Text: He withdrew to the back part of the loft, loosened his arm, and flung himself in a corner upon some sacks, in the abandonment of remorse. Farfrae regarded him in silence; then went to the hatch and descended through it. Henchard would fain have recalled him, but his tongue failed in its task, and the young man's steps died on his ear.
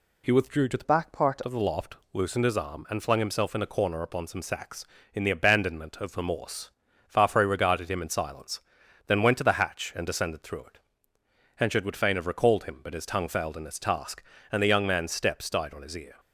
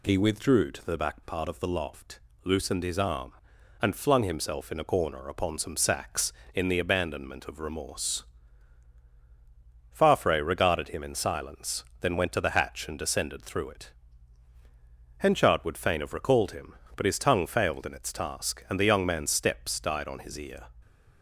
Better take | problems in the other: second | changes voice from "back" to "part"; from 0.8 to 1.4 s; 0.6 s long

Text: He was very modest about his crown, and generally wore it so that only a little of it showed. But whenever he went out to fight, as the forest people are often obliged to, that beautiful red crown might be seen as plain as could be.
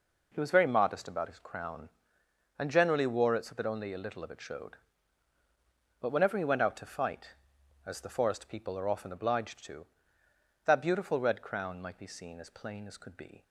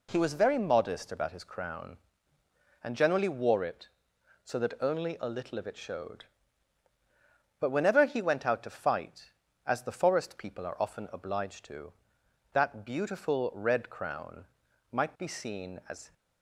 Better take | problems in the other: first | pauses between "crown" and "might"; noticeable; at 14.4 s; 0.46 s long // stops before "plain as could be"; at 16.1 s

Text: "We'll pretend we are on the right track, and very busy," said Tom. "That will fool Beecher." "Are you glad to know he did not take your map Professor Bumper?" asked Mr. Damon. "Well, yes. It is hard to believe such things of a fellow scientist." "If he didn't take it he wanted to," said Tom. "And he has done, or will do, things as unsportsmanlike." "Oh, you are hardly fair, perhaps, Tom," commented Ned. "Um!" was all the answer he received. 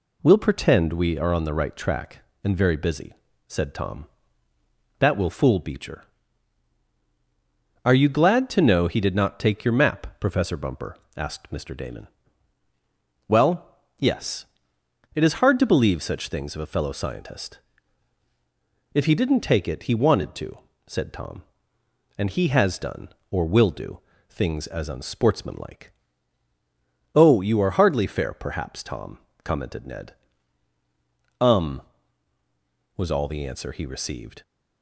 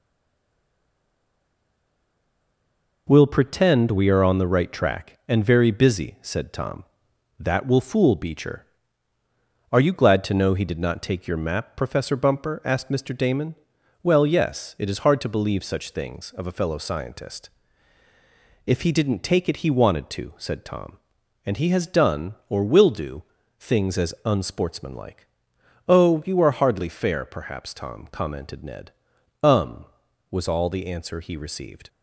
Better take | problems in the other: first | stays silent before the first word; strong; until 3.0 s; 3.0 s long

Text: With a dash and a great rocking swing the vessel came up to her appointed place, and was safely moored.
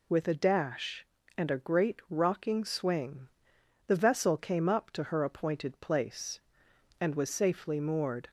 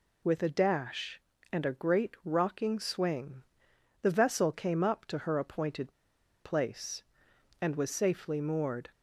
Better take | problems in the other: first | pauses between "swing" and "the"; noticeable; at 3.4 s; 0.60 s long; noticeable in the first // pauses between "appointed" and "place"; noticeable; at 5.9 s; 0.50 s long

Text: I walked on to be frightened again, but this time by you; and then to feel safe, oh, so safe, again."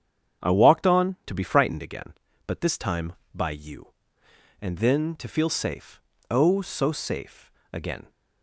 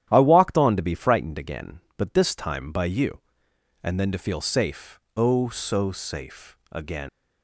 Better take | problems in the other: first | starts louder than the rest; strong; until 1.1 s; 11 dB; strong in the first // leaves "again" unfinished; at 7.0 s; 105 ms

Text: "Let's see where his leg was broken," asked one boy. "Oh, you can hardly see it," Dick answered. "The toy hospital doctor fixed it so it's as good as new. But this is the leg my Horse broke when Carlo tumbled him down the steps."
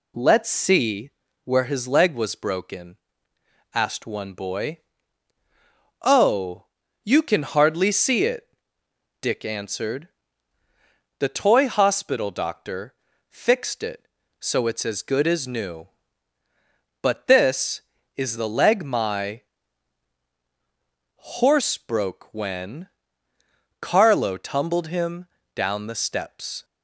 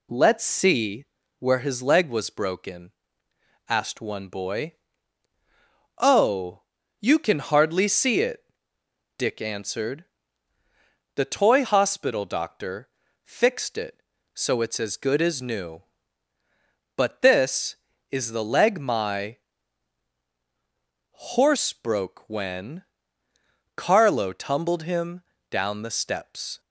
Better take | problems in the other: neither | pauses between "see" and "where"; slight; the same in both // pauses between "doctor" and "fixed"; slight; the same in both // pauses between "my" and "Horse"; strong; the same in both // pauses between "when" and "Carlo"; noticeable; the same in both // pauses between "him" and "down"; slight; the same in both

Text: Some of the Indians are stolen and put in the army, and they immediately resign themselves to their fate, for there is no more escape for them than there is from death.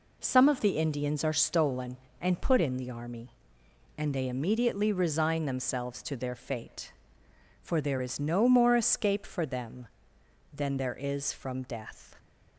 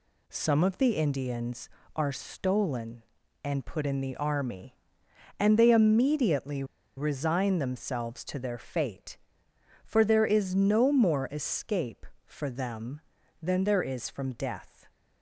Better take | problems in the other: first | pauses between "immediately" and "resign"; slight; at 6.6 s; 0.32 s long

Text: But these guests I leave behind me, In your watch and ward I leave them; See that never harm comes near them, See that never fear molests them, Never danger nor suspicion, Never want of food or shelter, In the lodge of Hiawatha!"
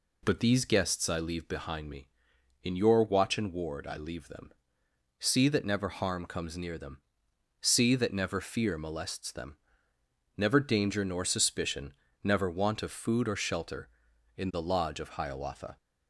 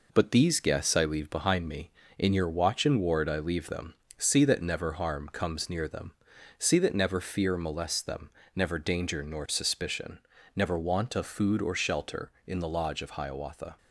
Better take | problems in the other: first | gets quieter; noticeable; throughout; 4 dB

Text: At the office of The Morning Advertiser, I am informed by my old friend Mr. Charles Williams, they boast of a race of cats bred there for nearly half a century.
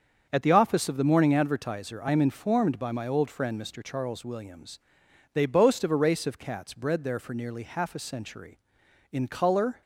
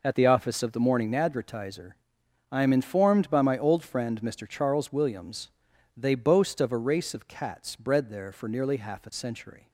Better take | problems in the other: second | starts louder than the rest; strong; until 1.3 s; 7 dB // goes on to say "In colour"; noticeable; from 9.1 s on; 0.70 s long

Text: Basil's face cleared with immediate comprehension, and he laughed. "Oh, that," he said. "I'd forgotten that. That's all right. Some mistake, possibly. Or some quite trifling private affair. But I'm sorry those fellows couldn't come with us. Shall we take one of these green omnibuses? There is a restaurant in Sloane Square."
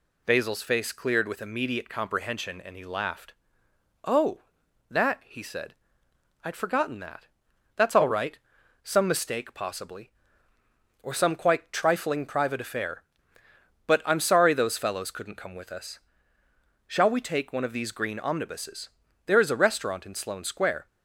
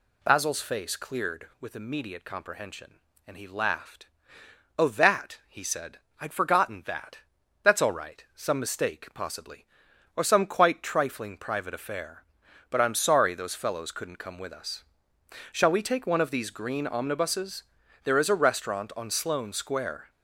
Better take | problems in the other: first | says "on" for "in"; at 18.9 s

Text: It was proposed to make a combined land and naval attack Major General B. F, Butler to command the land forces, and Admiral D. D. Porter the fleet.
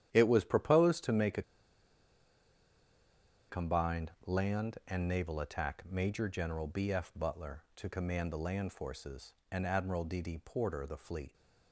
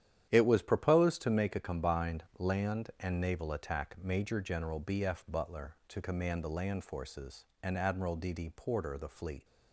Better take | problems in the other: second | starts louder than the rest; strong; until 1.1 s; 10.5 dB; strong in the second // pauses between "a" and "combined"; strong; at 1.4 s; 2.0 s long // pauses between "combined" and "land"; slight; at 4.1 s; 0.16 s long; slight in the second

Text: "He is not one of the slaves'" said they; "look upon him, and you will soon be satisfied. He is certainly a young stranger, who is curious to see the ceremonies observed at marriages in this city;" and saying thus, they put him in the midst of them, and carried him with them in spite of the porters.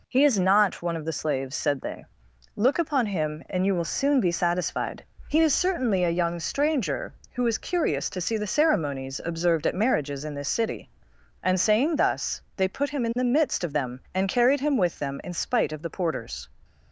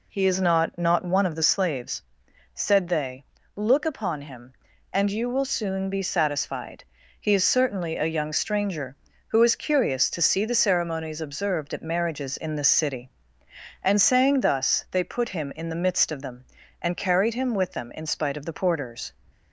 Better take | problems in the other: first | says "not" twice; at 0.7 s // pauses between "slaves" and "said"; noticeable; at 2.0 s; 0.50 s long

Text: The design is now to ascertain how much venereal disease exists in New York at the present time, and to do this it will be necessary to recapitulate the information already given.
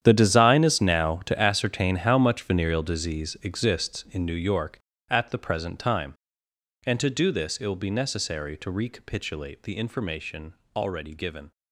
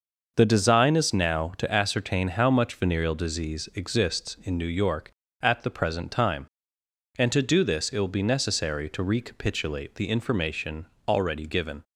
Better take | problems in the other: second | gets quieter; strong; throughout; 16 dB // starts louder than the rest; strong; until 1.0 s; 9.5 dB; noticeable in the second // pauses between "information" and "already"; slight; at 10.5 s; 0.20 s long; slight in the second

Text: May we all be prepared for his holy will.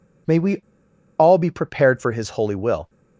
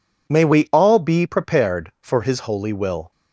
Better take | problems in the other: second | pauses between "we" and "all"; noticeable; at 0.5 s; 0.61 s long

